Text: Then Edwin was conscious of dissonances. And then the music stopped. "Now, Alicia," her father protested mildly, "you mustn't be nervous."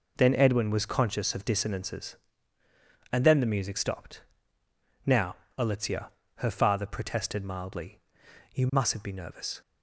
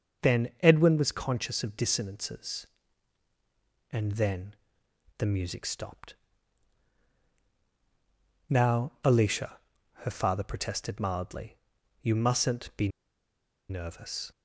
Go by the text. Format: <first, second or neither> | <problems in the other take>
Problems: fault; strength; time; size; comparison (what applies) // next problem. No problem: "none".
first | starts louder than the rest; until 1.3 s; 6.5 dB // pauses between "then" and "the"; noticeable; at 4.5 s; 0.64 s long // pauses between "be" and "nervous"; noticeable; at 12.8 s; 0.81 s long